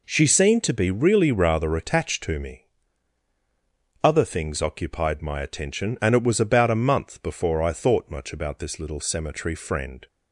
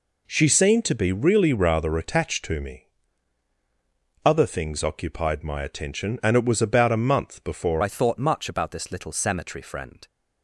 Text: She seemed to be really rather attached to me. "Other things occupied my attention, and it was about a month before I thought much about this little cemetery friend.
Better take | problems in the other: first | changes voice at "I"; from 7.8 s on; 2.2 s long

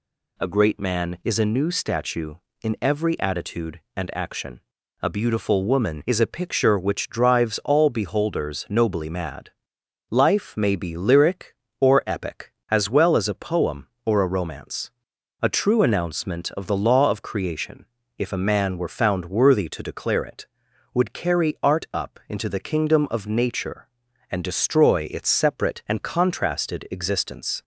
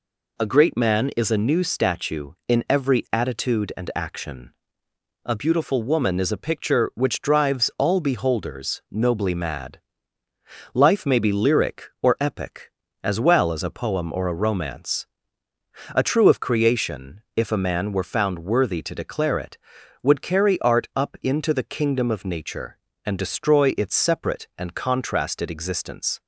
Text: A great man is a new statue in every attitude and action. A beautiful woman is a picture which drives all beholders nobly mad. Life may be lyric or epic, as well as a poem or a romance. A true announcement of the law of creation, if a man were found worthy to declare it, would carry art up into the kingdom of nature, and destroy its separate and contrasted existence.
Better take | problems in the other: first | skips "announcement of the law"; at 16.2 s

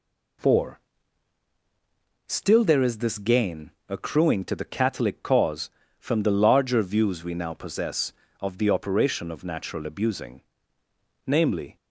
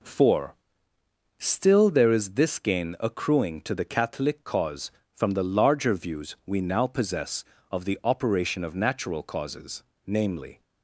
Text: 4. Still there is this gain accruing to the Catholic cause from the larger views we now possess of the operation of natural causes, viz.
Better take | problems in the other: second | pauses between "gain" and "accruing"; slight; at 3.7 s; 0.18 s long // says "abusing" for "causes"; at 9.8 s

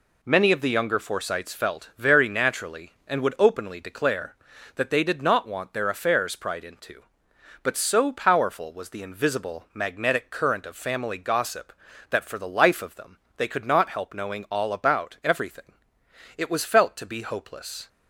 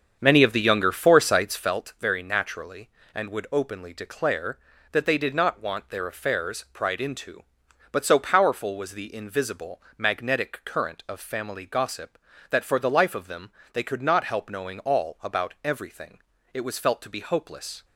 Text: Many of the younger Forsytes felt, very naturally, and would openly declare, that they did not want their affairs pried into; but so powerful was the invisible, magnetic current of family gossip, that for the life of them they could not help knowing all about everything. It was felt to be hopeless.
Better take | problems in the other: first | starts louder than the rest; strong; until 1.8 s; 7.5 dB // pauses between "them" and "they"; slight; at 13.5 s; 0.22 s long; slight in the first

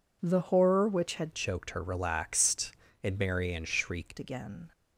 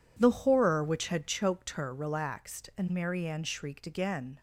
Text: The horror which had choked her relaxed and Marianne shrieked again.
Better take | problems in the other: second | changes voice from "choked" to "shrieked"; from 1.3 to 4.1 s; 2.8 s long

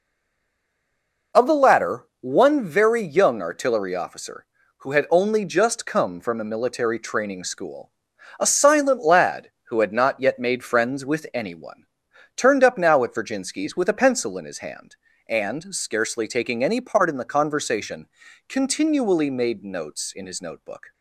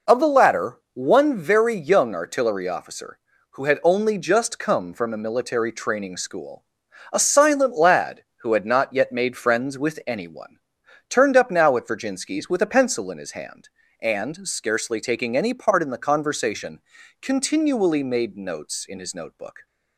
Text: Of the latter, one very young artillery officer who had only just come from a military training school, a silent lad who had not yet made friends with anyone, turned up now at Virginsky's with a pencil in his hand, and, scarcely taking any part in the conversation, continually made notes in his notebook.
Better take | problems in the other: second | stays silent before the first word; noticeable; until 1.3 s; 1.3 s long

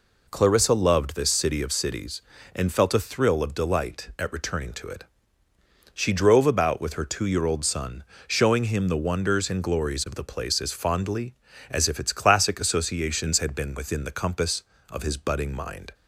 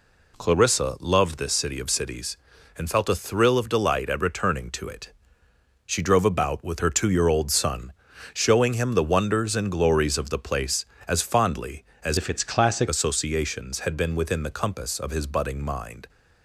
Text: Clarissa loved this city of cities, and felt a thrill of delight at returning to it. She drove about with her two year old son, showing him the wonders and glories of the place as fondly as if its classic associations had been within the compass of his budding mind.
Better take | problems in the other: first | changes voice from "if" to "classic"; from 12.1 to 12.8 s; 0.7 s long

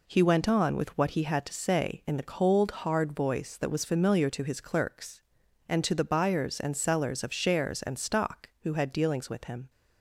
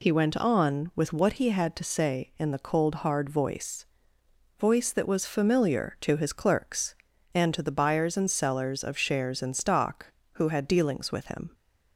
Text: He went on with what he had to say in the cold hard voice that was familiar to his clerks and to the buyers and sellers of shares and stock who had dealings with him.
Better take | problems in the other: first | says "voice" twice; at 4.5 s

